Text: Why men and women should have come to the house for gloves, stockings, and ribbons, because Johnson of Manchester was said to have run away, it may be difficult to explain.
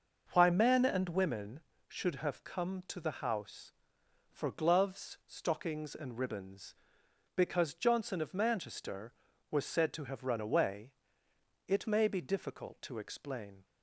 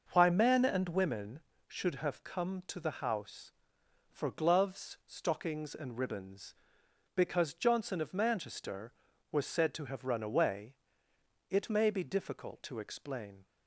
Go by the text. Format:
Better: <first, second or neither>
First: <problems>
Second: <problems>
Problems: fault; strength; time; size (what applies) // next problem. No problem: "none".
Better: neither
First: starts louder than the rest; noticeable; until 1.3 s; 6 dB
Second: starts louder than the rest; noticeable; until 1.1 s; 6 dB